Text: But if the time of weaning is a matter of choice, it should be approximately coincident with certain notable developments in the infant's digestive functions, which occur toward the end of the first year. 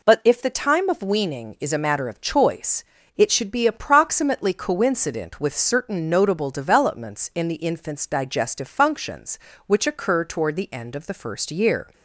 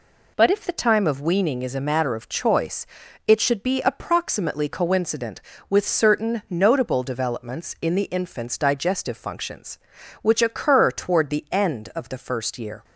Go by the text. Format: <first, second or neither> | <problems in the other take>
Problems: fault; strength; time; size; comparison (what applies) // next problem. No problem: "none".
neither | none